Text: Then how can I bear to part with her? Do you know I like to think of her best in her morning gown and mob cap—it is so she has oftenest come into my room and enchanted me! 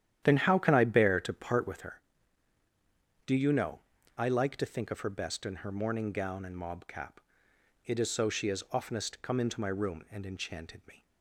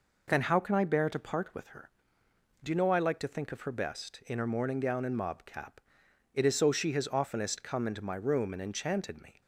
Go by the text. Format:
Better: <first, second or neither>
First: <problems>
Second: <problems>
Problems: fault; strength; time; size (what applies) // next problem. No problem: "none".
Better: second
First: starts louder than the rest; strong; until 1.9 s; 10.5 dB // pauses between "know" and "I"; slight; at 3.8 s; 0.36 s long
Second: none